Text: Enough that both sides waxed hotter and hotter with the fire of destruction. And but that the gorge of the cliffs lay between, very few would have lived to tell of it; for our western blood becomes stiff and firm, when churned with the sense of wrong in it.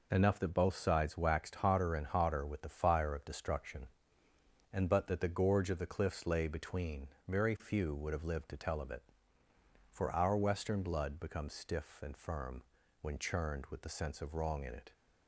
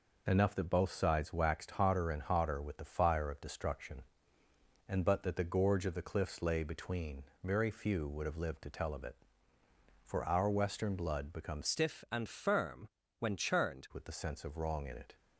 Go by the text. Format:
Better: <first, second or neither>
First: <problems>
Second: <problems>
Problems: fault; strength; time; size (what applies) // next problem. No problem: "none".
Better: first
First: none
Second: changes voice from "stiff" to "churned"; from 11.6 to 13.8 s; 2.2 s long